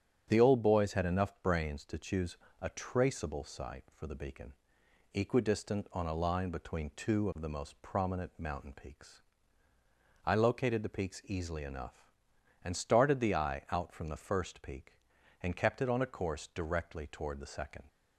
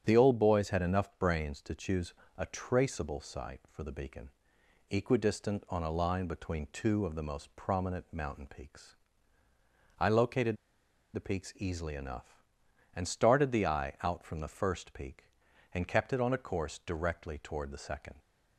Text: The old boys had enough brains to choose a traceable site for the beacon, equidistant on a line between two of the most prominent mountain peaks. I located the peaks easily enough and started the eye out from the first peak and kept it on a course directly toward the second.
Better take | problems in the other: first | starts louder than the rest; strong; until 1.0 s; 8.5 dB; strong in the first // pauses between "choose" and "a"; slight; at 2.1 s; 0.24 s long; slight in the first // pauses between "located" and "the"; noticeable; at 10.5 s; 0.58 s long

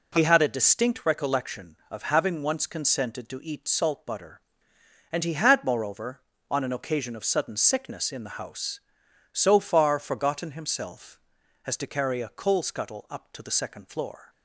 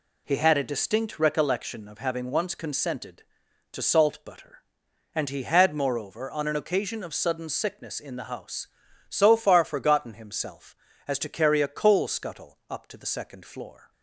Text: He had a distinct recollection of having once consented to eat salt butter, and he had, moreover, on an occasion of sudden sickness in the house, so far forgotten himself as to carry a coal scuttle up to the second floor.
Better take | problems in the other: first | skips "eat"; at 3.8 s

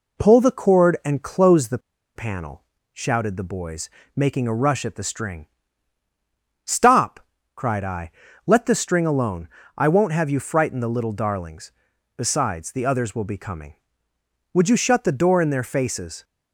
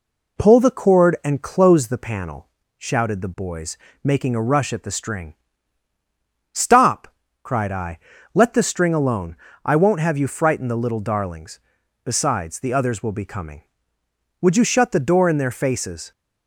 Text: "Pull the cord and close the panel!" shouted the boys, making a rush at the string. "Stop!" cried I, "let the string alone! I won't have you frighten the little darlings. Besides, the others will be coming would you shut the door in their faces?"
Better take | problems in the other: second | pauses between "the" and "panel"; at 1.7 s; 0.36 s long

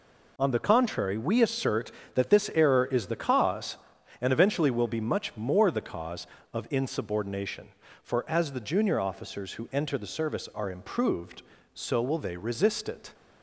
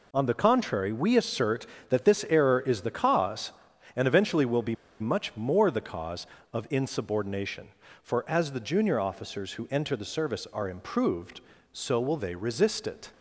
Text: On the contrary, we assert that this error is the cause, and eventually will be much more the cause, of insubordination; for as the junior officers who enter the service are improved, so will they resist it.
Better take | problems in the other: first | pauses between "be" and "much"; slight; at 4.7 s; 0.25 s long

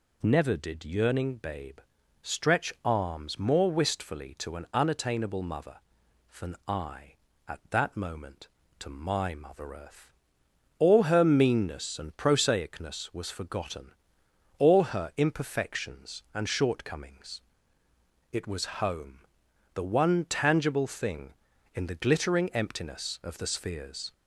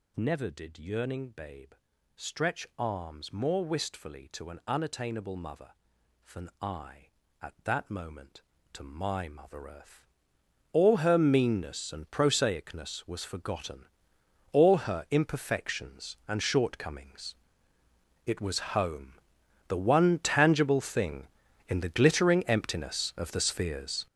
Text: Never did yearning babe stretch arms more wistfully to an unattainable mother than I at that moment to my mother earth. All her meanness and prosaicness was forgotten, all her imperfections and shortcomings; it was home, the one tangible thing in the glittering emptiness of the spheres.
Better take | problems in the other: first | gets louder; strong; throughout; 10 dB // pauses between "babe" and "stretch"; at 1.7 s; 0.42 s long; also in the first

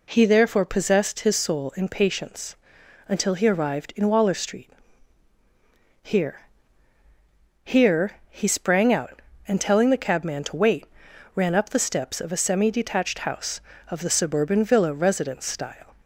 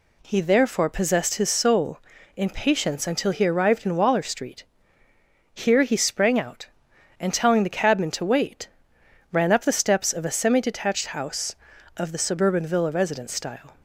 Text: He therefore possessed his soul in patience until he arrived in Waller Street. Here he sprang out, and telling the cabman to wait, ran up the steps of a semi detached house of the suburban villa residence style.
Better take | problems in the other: second | pauses between "patience" and "until"; noticeable; at 2.5 s; 0.52 s long // says "Here" twice; at 7.6 s

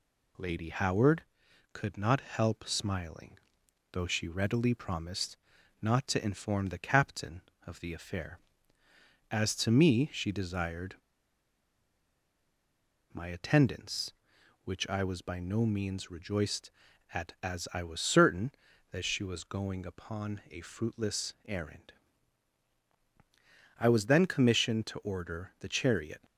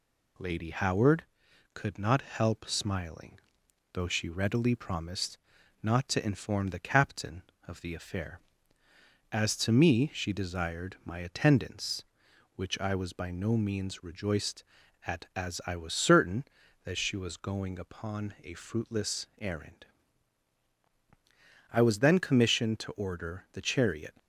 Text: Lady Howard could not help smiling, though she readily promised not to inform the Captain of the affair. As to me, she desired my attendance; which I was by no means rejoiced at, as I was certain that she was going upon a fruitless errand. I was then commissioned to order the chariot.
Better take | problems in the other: second | pauses between "promised" and "not"; at 5.3 s; 0.44 s long; also in the second // pauses between "desired" and "my"; strong; at 10.9 s; 2.1 s long

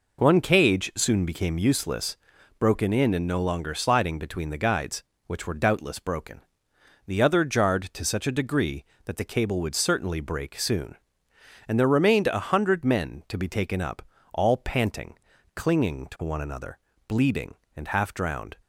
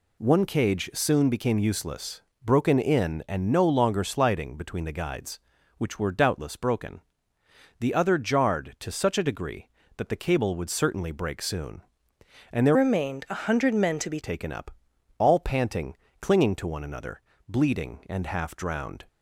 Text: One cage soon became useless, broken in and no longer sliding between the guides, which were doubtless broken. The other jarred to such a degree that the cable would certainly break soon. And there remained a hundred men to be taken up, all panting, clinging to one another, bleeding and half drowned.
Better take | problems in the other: first | changes voice from "remained" to "be"; from 12.7 to 14.1 s; 1.4 s long

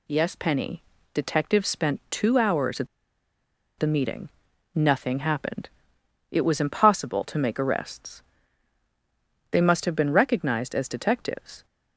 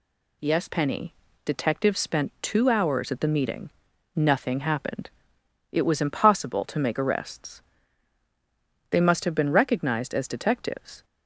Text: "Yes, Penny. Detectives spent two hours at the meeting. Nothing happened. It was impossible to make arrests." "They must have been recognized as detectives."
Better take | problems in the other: second | pauses between "at" and "the"; noticeable; at 2.8 s; 0.93 s long

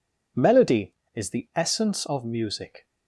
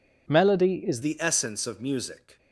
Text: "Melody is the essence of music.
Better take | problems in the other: first | changes voice at "the"; from 1.0 s on; 1.3 s long

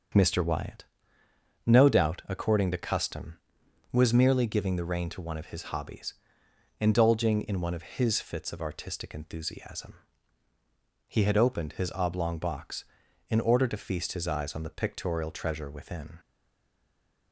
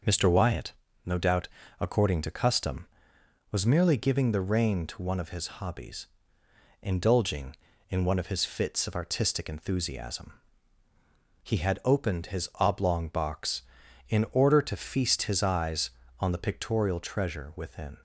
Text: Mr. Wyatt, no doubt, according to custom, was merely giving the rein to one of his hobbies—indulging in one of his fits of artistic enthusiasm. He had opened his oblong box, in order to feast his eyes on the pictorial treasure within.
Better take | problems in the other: second | starts louder than the rest; until 1.9 s; 6.5 dB; noticeable in the second // stays silent after the last word; from 16.1 s on; 1.2 s long

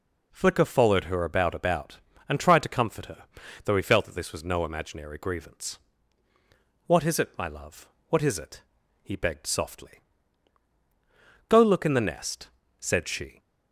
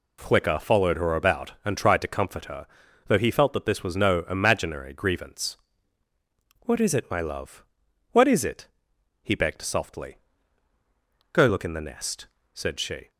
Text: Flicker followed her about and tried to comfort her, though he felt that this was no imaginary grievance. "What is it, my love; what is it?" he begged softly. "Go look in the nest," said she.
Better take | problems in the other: second | says "about" twice; at 1.5 s

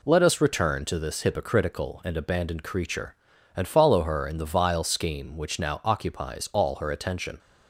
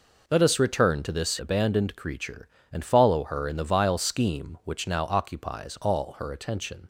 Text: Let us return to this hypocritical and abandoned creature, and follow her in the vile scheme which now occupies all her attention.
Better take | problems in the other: first | skips "hypocritical and"; at 1.3 s

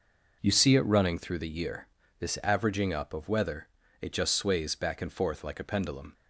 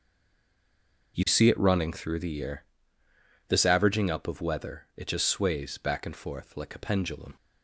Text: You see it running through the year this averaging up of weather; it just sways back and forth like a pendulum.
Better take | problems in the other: first | stays silent before the first word; until 1.1 s; 1.1 s long // pauses between "year" and "this"; noticeable; at 2.6 s; 0.86 s long; slight in the first

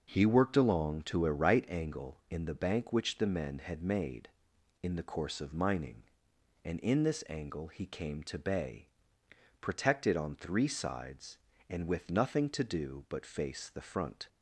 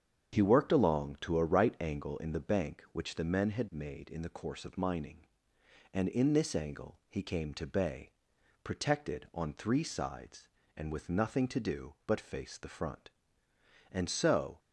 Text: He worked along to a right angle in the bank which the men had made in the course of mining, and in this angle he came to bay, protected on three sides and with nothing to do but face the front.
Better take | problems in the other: first | starts louder than the rest; strong; until 1.3 s; 8 dB // goes on to say "And so"; noticeable; from 13.9 s on; 0.68 s long

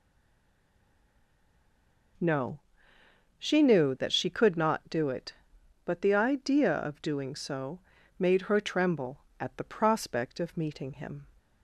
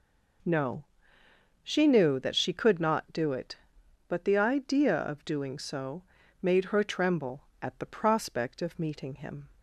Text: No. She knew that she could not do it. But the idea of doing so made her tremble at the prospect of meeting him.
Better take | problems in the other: second | stays silent before the first word; until 2.1 s; 2.1 s long // pauses between "so" and "made"; at 7.7 s; 0.38 s long; also in the second

